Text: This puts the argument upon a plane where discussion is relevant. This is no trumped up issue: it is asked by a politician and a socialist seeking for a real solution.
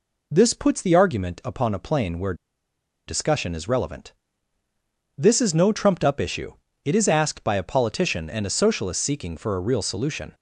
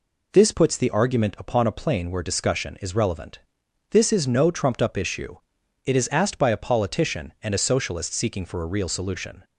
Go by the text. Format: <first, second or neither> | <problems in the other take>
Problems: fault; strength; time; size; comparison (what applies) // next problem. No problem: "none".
second | pauses between "where" and "discussion"; noticeable; at 2.3 s; 0.73 s long